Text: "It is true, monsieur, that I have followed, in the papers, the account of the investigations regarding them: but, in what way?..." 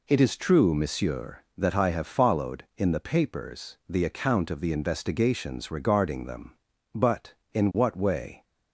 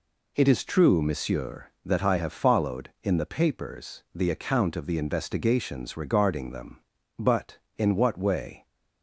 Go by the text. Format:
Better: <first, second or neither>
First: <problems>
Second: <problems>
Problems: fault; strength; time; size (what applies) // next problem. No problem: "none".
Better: neither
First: none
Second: none